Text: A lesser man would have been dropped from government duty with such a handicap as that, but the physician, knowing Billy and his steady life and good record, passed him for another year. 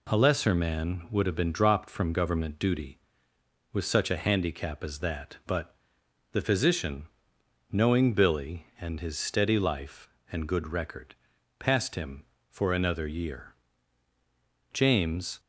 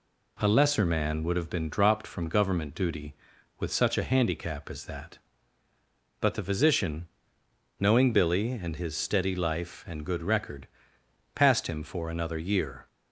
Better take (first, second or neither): second